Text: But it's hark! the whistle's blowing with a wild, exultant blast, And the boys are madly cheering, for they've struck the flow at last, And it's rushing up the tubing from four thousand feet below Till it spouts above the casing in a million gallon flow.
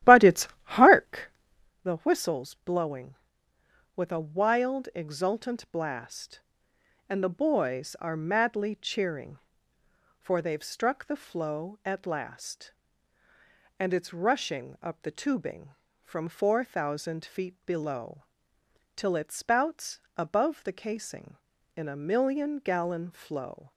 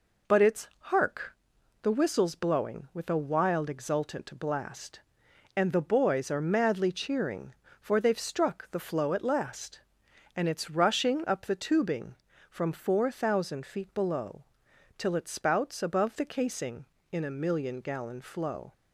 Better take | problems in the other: second | starts louder than the rest; strong; until 1.7 s; 14 dB // pauses between "below" and "Till"; noticeable; at 18.2 s; 0.74 s long; noticeable in the second // pauses between "spouts" and "above"; slight; at 20.0 s; 0.16 s long

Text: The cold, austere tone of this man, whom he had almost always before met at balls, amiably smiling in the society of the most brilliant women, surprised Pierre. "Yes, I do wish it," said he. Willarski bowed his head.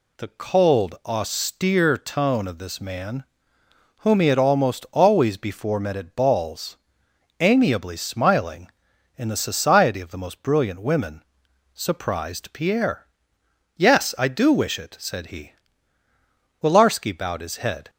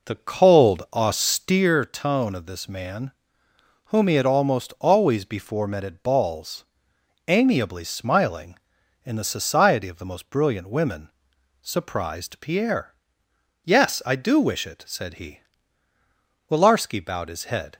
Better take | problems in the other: first | starts louder than the rest; noticeable; until 1.7 s; 4.5 dB

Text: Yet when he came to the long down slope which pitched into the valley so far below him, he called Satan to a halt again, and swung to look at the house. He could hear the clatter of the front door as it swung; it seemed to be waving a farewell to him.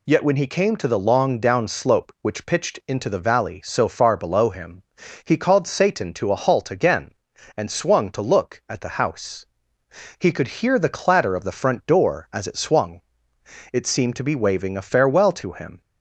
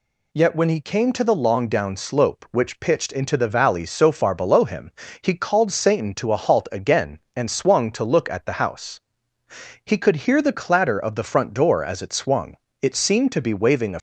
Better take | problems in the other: first | stops before "farewell to him"; at 13.9 s

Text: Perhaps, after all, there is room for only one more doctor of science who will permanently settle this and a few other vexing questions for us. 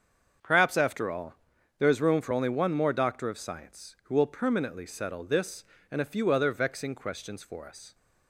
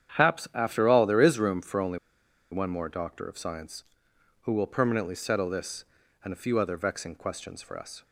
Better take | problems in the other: first | starts louder than the rest; strong; until 1.2 s; 9 dB; also in the first // pauses between "only" and "one"; noticeable; at 1.9 s; 0.55 s long

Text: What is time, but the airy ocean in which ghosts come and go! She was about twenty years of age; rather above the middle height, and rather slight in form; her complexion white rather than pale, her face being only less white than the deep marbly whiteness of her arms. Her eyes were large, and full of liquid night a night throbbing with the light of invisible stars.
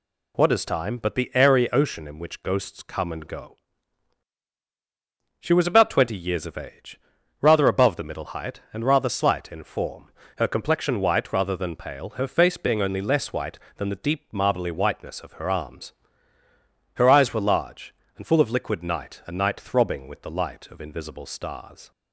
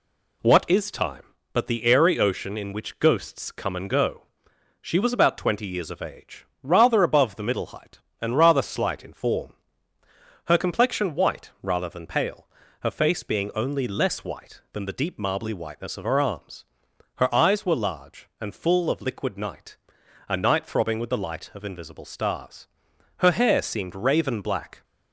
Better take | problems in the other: first | pauses between "night" and "a"; noticeable; at 19.7 s; 0.54 s long // goes on to say "Her hair seemed raven black"; from 23.1 s on; 1.6 s long

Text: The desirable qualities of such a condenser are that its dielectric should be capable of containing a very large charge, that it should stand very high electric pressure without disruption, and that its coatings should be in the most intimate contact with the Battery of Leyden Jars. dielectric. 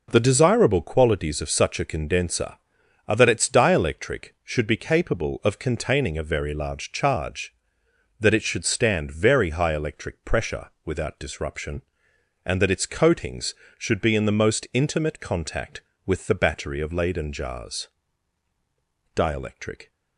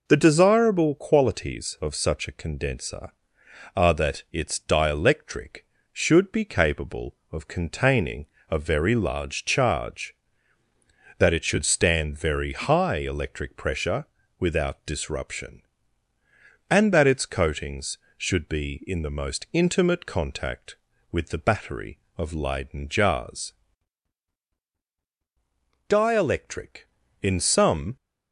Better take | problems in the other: first | pauses between "containing" and "a"; slight; at 8.2 s; 0.24 s long // pauses between "pressure" and "without"; slight; at 14.0 s; 0.34 s long // goes on to say "In some"; noticeable; from 27.2 s on; 0.74 s long

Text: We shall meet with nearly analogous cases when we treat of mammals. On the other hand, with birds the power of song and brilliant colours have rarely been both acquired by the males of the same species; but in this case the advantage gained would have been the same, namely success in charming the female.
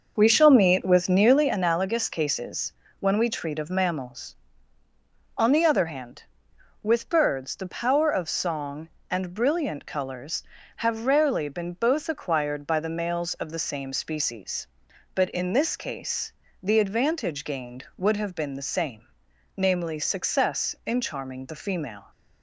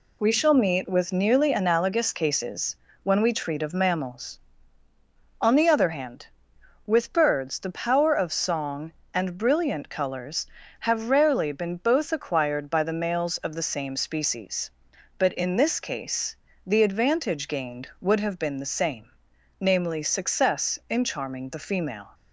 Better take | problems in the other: second | starts louder than the rest; noticeable; until 1.5 s; 6 dB // pauses between "cases" and "when"; slight; at 2.7 s; 0.28 s long; slight in the second // pauses between "case" and "the"; slight; at 16.3 s; 0.30 s long; slight in the second

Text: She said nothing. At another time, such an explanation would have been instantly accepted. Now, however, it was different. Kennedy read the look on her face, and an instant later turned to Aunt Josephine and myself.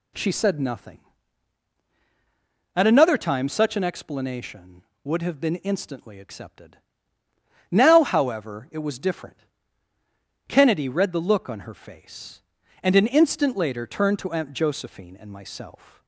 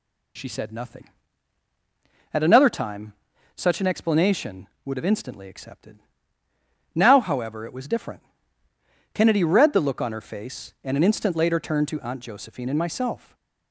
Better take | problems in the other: first | skips "been"; at 5.1 s // stays silent after the last word; slight; from 13.1 s on; 0.6 s long

